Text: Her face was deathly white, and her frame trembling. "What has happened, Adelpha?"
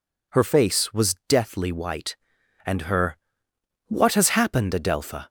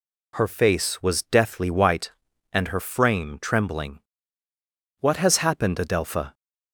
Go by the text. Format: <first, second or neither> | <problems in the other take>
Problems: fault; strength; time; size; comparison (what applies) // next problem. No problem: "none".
second | skips "frame trembling"; at 3.5 s